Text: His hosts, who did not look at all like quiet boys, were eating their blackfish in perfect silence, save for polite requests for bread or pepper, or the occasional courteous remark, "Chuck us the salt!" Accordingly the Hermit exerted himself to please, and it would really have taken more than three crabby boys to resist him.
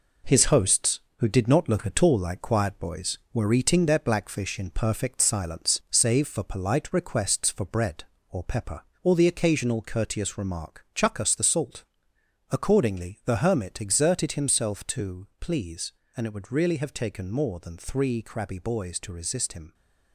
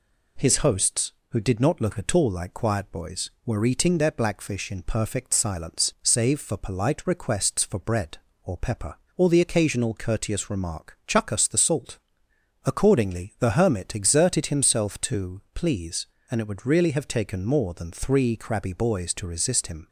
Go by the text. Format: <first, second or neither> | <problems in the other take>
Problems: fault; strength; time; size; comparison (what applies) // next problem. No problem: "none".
second | gets quieter; noticeable; throughout; 5 dB